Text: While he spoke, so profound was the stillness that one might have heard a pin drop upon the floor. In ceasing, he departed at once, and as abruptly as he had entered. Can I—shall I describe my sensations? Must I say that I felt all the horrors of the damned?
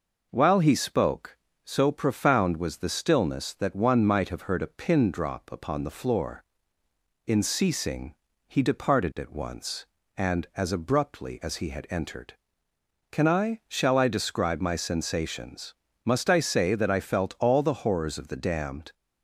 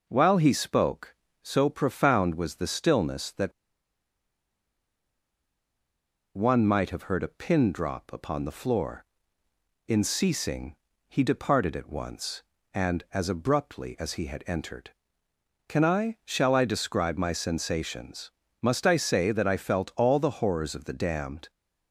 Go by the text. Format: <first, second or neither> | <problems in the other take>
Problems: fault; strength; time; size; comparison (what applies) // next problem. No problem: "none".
first | pauses between "that" and "one"; strong; at 3.5 s; 2.8 s long